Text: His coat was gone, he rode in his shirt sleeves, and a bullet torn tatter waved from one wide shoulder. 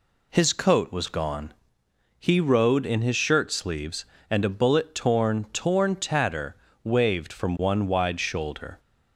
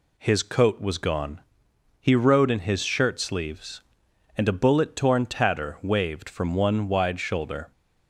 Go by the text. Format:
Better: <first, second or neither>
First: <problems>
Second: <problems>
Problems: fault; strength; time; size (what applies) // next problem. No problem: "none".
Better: second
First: says "torn" twice; at 5.5 s // pauses between "tatter" and "waved"; slight; at 6.5 s; 0.30 s long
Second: none